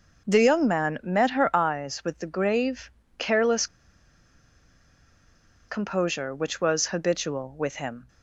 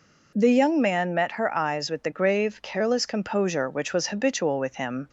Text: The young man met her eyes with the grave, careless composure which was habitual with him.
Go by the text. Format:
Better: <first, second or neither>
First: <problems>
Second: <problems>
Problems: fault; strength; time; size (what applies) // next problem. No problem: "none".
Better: second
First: pauses between "careless" and "composure"; strong; at 3.6 s; 2.0 s long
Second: none